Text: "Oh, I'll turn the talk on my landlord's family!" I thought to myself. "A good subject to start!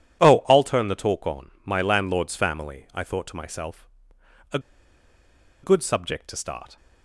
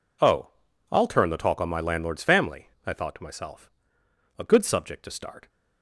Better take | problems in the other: second | pauses between "A" and "good"; at 4.5 s; 1.0 s long

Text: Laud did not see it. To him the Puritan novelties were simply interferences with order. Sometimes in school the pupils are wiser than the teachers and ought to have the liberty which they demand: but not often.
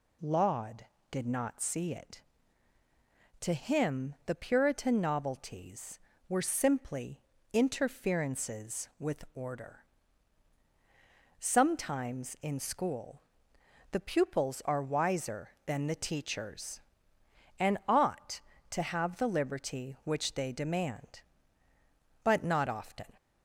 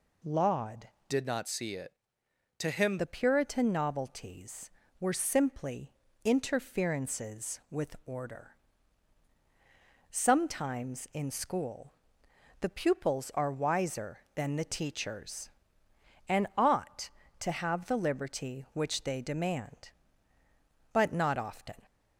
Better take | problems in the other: first | changes voice from "did" to "him"; from 1.0 to 2.9 s; 1.9 s long // pauses between "simply" and "interferences"; slight; at 5.9 s; 0.32 s long; slight in the first // pauses between "school" and "the"; noticeable; at 11.9 s; 0.68 s long; noticeable in the first

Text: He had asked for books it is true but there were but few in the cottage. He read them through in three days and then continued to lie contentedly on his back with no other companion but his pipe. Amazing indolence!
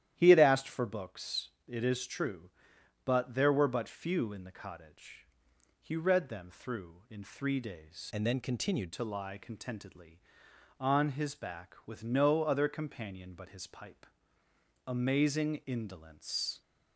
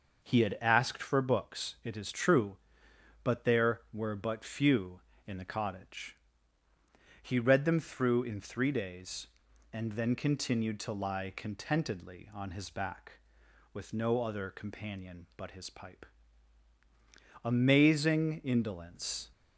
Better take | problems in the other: second | starts louder than the rest; strong; until 1.1 s; 11.5 dB // pauses between "books" and "it"; slight; at 1.5 s; 0.18 s long // changes voice from "and" to "continued"; from 8.1 to 8.9 s; 0.8 s long

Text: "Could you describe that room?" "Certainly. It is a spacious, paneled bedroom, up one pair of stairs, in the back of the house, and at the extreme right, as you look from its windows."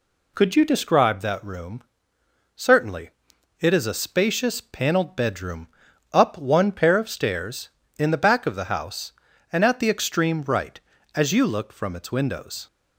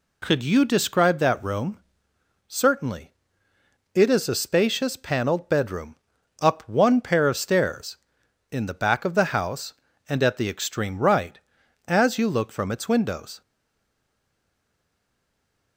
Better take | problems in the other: first | stays silent after the last word; from 13.4 s on; 2.3 s long

